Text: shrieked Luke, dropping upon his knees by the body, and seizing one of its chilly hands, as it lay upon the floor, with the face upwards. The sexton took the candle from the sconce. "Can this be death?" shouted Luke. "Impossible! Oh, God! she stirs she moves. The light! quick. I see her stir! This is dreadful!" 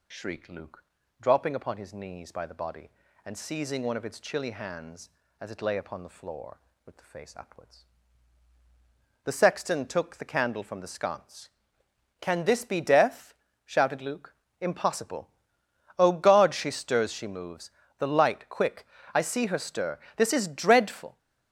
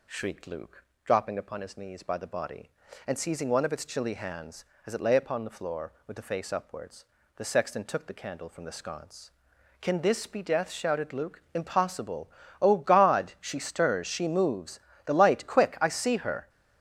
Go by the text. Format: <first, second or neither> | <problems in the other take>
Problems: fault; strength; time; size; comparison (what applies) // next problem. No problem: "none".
first | stops before "stir This is dreadful"; at 16.4 s